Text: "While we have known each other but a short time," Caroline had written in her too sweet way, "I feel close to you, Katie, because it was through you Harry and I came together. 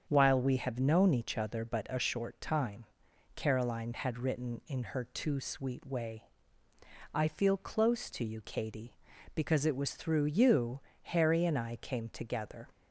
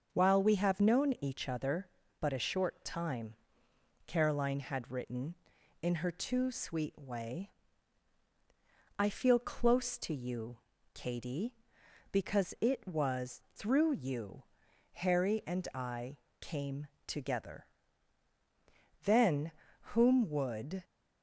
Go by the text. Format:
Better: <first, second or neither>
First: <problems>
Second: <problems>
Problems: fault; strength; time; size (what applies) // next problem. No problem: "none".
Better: first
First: starts louder than the rest; strong; until 1.0 s; 7.5 dB // pauses between "you" and "Harry"; slight; at 10.7 s; 0.22 s long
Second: starts louder than the rest; until 1.1 s; 6.5 dB // pauses between "you" and "Harry"; noticeable; at 14.4 s; 0.52 s long // pauses between "I" and "came"; slight; at 16.1 s; 0.22 s long // goes on to say "Then whom would"; strong; from 19.0 s on; 1.8 s long